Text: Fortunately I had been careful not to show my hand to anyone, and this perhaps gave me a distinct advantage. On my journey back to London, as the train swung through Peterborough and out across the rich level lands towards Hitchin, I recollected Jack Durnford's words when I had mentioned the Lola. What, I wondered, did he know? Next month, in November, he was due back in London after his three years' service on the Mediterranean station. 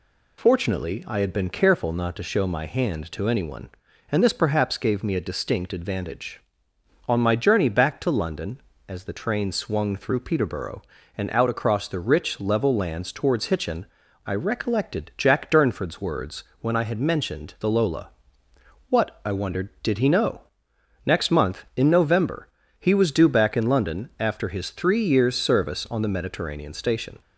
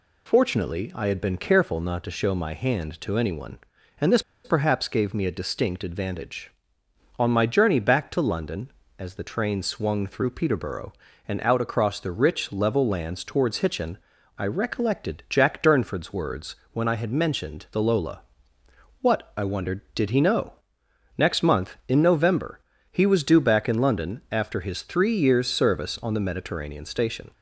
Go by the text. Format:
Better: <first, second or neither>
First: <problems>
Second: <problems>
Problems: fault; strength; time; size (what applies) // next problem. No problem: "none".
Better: first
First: pauses between "words" and "when"; slight; at 16.4 s; 0.18 s long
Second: pauses between "this" and "perhaps"; slight; at 4.2 s; 0.23 s long // pauses between "words" and "when"; slight; at 16.5 s; 0.18 s long